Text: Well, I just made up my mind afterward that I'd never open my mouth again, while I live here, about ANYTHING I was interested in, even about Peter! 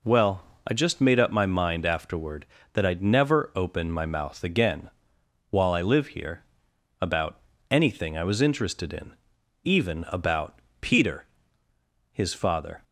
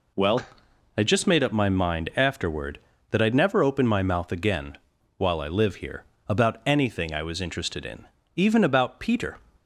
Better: second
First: pauses between "about" and "ANYTHING"; slight; at 7.3 s; 0.32 s long // pauses between "about" and "Peter"; slight; at 10.5 s; 0.22 s long // goes on to say "His father"; noticeable; from 12.1 s on; 0.72 s long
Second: none

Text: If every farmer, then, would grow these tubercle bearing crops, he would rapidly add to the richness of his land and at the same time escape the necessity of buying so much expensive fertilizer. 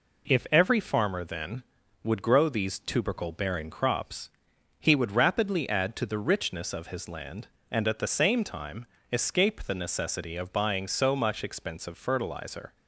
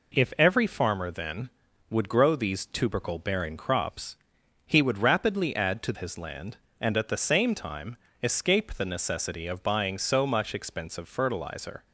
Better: first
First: pauses between "time" and "escape"; slight; at 8.8 s; 0.26 s long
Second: skips "the richness of"; at 5.9 s // pauses between "time" and "escape"; slight; at 7.9 s; 0.26 s long

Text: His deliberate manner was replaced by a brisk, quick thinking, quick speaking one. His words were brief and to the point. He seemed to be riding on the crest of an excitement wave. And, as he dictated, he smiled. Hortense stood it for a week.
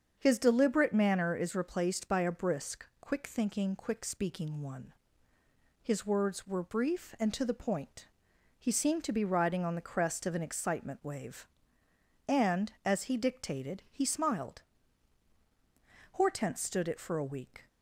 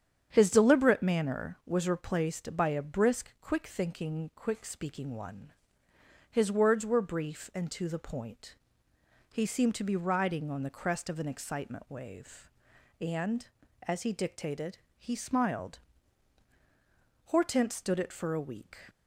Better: second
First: starts louder than the rest; strong; until 1.2 s; 7 dB // says "is" for "was"; at 1.3 s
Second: starts louder than the rest; strong; until 1.3 s; 8.5 dB

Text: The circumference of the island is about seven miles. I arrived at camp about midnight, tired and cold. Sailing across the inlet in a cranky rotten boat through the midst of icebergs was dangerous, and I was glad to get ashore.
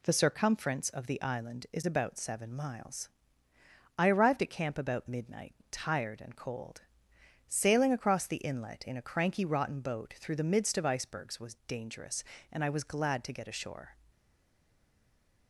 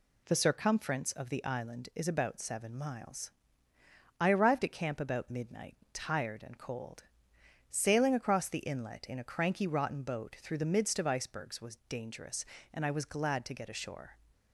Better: second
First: stays silent after the last word; noticeable; from 14.1 s on; 1.3 s long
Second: none

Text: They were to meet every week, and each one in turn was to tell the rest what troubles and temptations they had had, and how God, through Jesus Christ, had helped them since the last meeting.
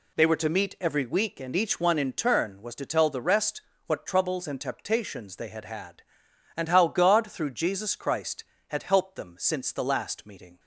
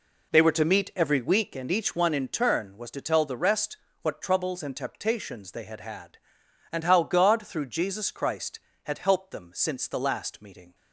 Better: first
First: pauses between "rest" and "what"; slight; at 3.6 s; 0.26 s long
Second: starts louder than the rest; until 1.7 s; 3.5 dB // pauses between "rest" and "what"; slight; at 3.7 s; 0.26 s long

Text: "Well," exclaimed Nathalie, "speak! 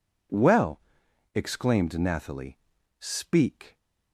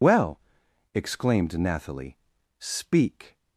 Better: first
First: none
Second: loses the start of "Well"; at 0.0 s; 115 ms

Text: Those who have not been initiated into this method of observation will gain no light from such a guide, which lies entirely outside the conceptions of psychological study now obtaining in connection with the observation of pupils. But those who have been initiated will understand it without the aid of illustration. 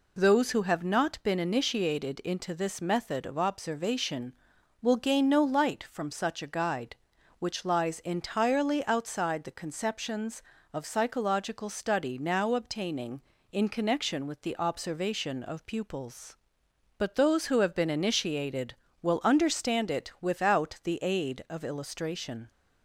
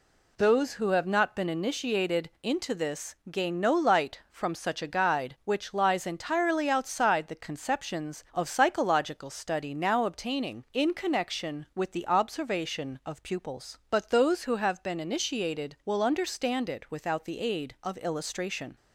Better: first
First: none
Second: skips "method of observation will"; at 3.2 s

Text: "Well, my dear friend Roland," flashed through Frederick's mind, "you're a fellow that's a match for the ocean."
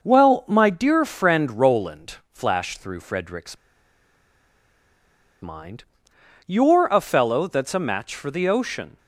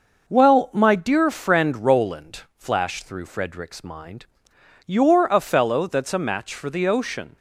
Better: second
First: pauses between "Frederick's" and "mind"; strong; at 3.5 s; 1.8 s long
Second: none

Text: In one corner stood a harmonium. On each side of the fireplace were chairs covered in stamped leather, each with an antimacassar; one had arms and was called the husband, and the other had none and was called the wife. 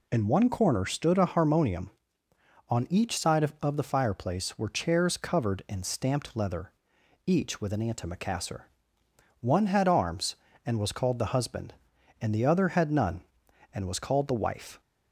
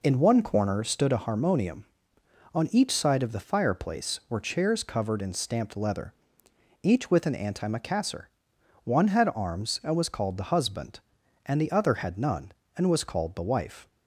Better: second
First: says "of" twice; at 3.6 s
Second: none

